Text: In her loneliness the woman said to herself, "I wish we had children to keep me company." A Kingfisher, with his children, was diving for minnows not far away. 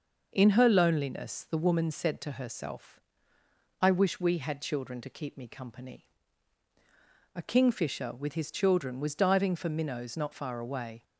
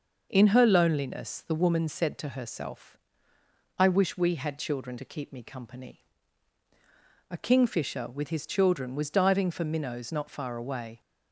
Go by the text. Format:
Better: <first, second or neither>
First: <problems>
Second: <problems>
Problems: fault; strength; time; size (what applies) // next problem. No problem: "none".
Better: neither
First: none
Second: none